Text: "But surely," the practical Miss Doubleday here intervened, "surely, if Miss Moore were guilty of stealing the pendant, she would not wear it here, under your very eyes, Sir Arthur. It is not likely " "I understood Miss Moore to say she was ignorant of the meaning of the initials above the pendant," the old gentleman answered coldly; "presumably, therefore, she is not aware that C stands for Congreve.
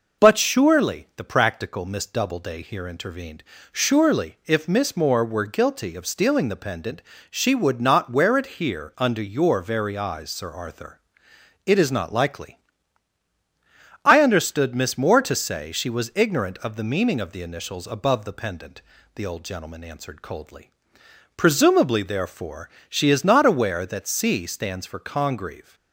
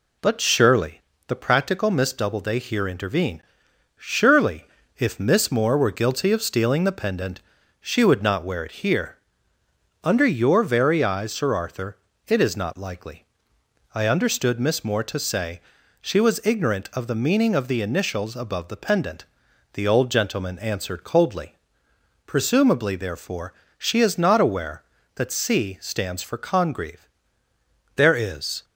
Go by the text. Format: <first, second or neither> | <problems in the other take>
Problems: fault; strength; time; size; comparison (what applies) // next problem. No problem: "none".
first | pauses between "say" and "she"; at 15.6 s; 0.40 s long // goes on to say "There is"; noticeable; from 27.9 s on; 0.68 s long